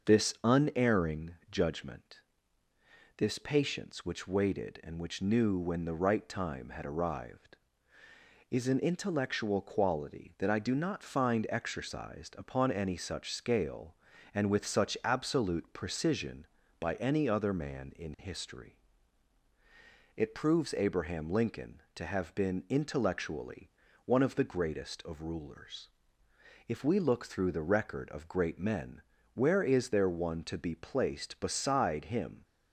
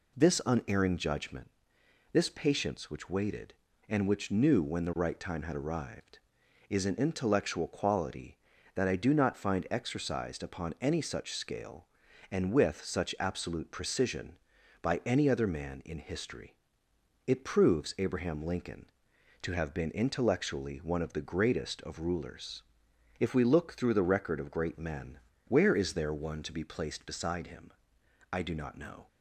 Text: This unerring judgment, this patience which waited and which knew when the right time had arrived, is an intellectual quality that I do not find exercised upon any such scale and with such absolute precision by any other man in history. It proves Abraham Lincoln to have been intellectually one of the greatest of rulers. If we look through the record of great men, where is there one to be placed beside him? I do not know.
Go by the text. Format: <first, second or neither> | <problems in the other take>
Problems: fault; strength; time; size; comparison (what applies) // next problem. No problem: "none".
second | starts louder than the rest; until 1.1 s; 6.5 dB // pauses between "intellectually" and "one"; at 23.6 s; 0.38 s long // stops before "I do not know"; at 32.4 s